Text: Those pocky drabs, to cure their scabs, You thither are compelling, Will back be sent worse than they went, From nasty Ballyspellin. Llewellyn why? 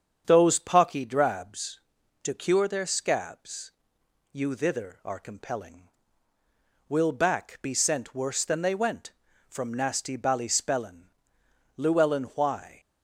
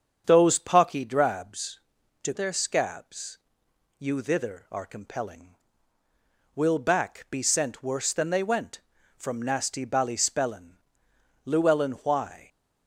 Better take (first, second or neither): first